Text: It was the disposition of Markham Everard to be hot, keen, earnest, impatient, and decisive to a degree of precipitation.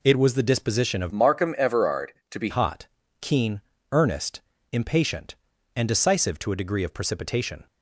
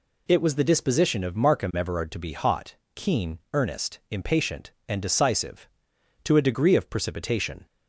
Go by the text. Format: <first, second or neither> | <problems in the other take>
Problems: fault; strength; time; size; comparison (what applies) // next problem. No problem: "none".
second | changes voice from "Markham" to "be"; from 1.1 to 2.4 s; 1.3 s long